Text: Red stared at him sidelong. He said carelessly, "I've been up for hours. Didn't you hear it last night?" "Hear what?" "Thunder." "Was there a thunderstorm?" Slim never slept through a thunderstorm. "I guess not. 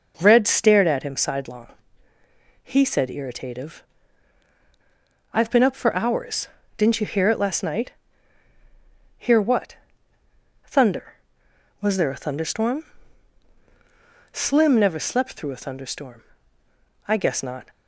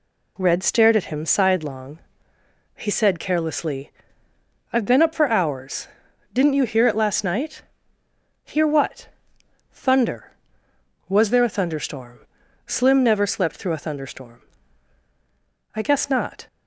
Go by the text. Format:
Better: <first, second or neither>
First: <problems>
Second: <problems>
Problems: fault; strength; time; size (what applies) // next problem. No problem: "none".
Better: second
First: says "irritative" for "carelessly"; at 3.0 s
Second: none